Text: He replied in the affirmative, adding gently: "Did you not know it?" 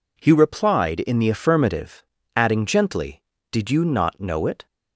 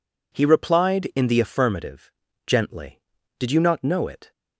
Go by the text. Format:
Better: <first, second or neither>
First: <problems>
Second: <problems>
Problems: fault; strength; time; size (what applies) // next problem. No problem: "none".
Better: first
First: none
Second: skips "adding"; at 2.2 s